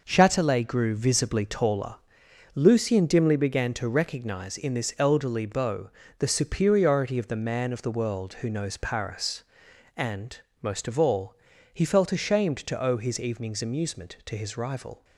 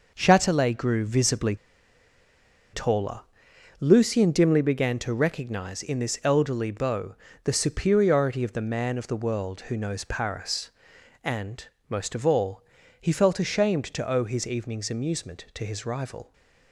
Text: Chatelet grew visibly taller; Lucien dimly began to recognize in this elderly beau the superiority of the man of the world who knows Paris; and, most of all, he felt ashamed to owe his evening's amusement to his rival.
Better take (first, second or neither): first